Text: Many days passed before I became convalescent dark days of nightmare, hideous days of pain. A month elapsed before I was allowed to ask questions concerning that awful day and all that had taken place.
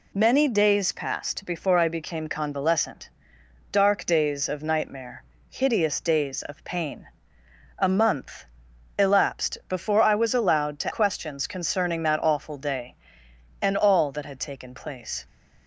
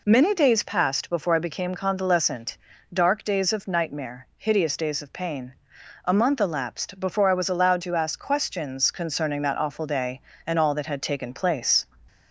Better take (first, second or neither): second